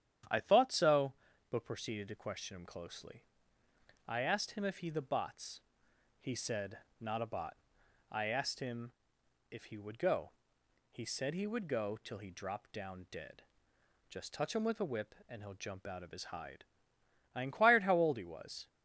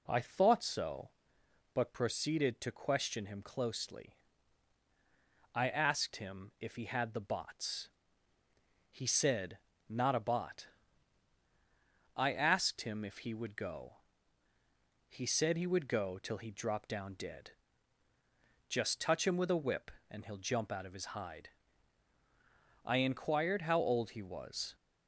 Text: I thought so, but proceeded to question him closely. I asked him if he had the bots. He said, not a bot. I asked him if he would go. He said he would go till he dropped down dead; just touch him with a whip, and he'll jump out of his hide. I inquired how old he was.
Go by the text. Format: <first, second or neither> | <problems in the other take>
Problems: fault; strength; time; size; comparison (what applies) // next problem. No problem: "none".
second | starts louder than the rest; strong; until 1.6 s; 9.5 dB // skips "had"; at 4.9 s // pauses between "him" and "if"; noticeable; at 8.9 s; 0.58 s long